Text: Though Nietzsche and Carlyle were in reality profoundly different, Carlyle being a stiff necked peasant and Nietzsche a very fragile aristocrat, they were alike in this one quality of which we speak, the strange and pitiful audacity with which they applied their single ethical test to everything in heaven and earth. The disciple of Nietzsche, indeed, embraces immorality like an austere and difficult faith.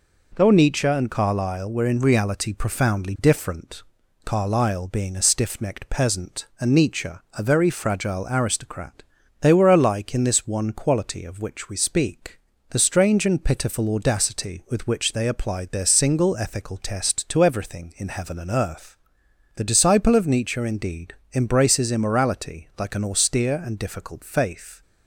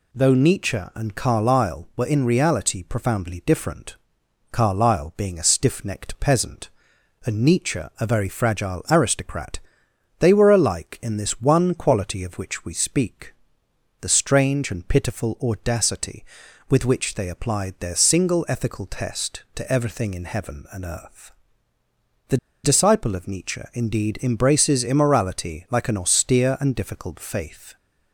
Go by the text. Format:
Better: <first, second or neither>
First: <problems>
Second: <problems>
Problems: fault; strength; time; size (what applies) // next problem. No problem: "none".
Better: first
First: none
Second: pauses between "The" and "disciple"; slight; at 22.3 s; 0.26 s long